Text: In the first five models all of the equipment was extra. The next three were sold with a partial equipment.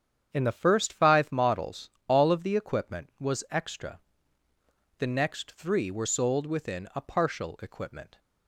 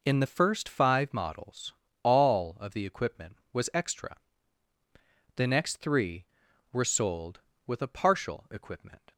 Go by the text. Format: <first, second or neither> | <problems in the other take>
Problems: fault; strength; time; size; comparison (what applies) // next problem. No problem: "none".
second | starts louder than the rest; strong; until 1.3 s; 8.5 dB // pauses between "models" and "all"; slight; at 1.8 s; 0.18 s long; slight in the second // says "within" for "with"; at 6.4 s